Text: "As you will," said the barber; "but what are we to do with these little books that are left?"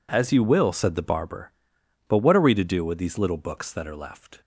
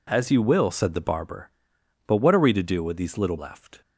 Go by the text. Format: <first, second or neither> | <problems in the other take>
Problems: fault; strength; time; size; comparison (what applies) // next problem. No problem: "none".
first | skips "books that are"; at 3.3 s